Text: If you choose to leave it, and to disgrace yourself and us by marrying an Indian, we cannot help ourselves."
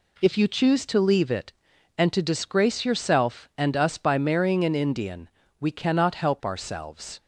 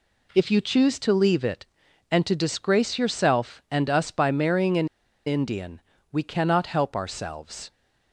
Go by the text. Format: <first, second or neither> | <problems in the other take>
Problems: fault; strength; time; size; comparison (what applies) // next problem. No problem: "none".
first | pauses between "an" and "Indian"; at 4.8 s; 0.38 s long